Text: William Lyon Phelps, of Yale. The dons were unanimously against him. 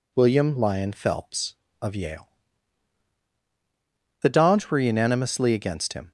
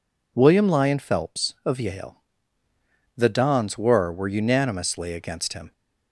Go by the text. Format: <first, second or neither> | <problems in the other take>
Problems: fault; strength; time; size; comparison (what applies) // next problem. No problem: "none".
first | says "were" twice; at 4.1 s